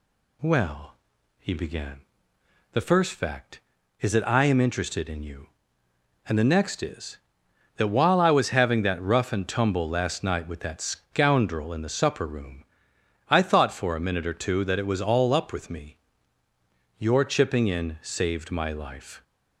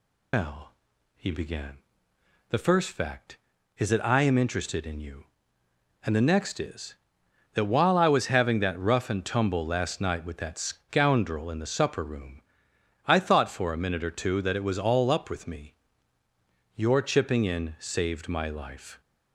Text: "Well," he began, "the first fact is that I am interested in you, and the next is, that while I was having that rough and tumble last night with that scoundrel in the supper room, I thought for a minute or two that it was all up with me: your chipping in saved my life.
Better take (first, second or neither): first